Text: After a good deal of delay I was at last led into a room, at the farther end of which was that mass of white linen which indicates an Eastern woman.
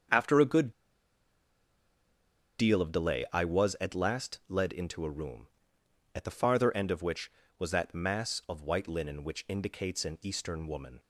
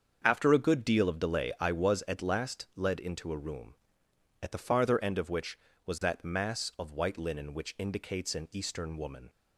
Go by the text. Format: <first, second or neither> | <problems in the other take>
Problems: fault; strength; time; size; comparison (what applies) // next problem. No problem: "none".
second | starts louder than the rest; until 2.9 s; 7 dB; also in the second // pauses between "good" and "deal"; strong; at 0.7 s; 1.8 s long